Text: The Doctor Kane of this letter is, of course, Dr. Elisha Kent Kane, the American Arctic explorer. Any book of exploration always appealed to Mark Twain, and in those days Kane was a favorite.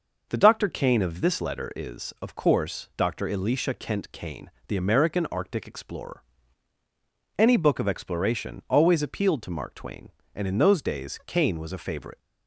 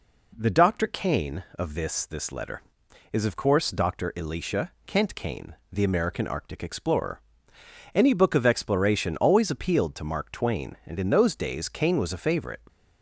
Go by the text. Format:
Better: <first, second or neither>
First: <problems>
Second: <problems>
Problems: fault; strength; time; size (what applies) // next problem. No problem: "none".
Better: first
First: none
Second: says "this" twice; at 2.0 s // pauses between "Elisha" and "Kent"; slight; at 4.7 s; 0.16 s long